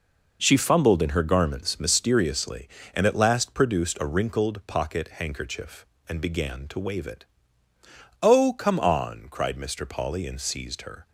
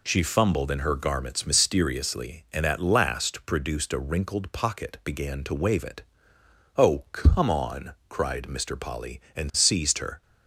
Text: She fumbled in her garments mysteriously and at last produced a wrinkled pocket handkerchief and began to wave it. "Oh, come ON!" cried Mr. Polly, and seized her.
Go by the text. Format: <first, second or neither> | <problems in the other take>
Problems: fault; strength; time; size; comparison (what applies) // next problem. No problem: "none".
first | skips "handkerchief and"; at 5.0 s